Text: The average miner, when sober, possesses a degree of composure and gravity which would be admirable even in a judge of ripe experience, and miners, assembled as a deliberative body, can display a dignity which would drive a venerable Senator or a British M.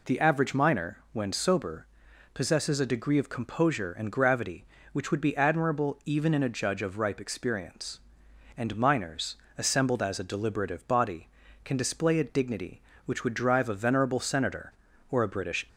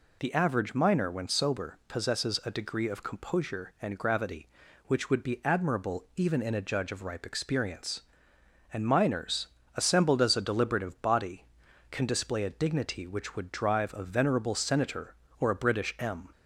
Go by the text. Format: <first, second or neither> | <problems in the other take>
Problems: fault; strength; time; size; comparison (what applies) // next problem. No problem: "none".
second | stops before "M"; at 15.6 s